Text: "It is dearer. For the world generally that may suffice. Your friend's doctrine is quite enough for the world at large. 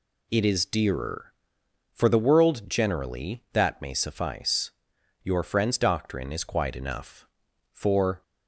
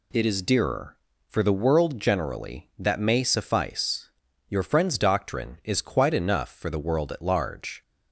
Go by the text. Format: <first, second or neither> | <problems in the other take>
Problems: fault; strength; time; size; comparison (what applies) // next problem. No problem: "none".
second | stops before "the world at large"; at 8.2 s